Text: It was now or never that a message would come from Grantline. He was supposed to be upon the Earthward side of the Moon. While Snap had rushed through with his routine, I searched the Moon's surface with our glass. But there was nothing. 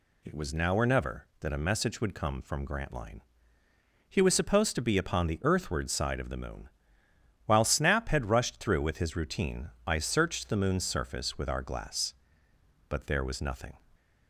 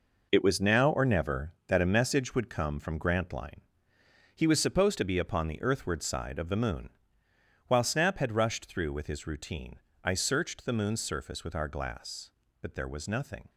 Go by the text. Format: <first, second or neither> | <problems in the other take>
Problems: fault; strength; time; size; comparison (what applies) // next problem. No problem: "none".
first | gets quieter; strong; throughout; 9.5 dB